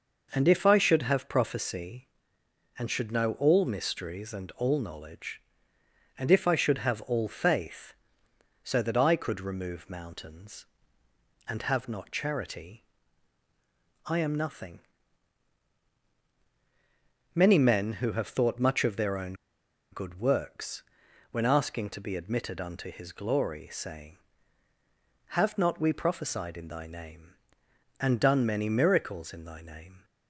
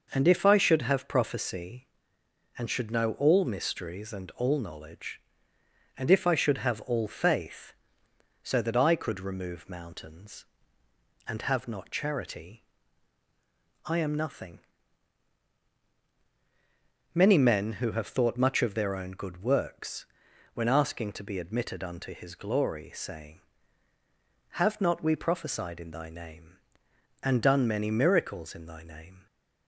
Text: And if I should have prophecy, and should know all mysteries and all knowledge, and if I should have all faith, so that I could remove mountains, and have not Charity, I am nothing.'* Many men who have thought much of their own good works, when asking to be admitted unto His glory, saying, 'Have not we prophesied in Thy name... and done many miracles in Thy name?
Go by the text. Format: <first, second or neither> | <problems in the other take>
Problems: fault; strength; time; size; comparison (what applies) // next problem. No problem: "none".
second | pauses between "own" and "good"; noticeable; at 19.3 s; 0.58 s long